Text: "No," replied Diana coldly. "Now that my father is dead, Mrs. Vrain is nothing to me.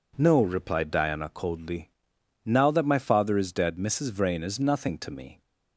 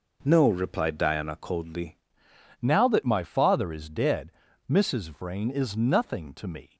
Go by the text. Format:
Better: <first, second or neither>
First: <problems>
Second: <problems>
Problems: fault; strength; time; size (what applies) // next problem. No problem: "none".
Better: first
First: none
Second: changes voice at "Now"; from 2.6 s on; 4.1 s long